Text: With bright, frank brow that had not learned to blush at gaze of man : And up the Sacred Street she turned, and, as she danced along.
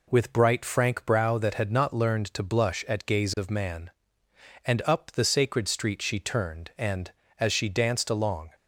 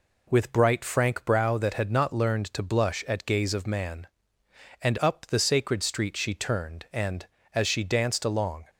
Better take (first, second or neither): neither